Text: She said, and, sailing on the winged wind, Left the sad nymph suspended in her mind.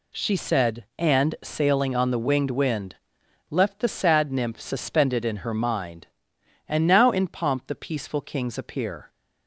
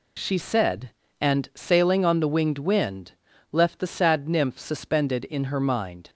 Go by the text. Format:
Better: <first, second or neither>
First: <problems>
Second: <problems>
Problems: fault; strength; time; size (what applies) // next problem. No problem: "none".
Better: second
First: goes on to say "And now in pomp the peaceful kings appear"; strong; from 6.6 s on; 2.4 s long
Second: none